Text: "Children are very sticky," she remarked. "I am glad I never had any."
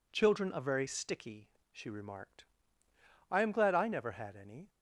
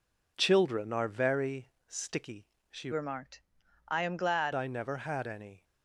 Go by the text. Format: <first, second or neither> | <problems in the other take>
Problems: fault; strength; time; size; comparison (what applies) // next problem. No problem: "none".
first | pauses between "very" and "sticky"; slight; at 1.7 s; 0.16 s long // changes voice from "remarked" to "glad"; from 2.9 to 4.5 s; 1.6 s long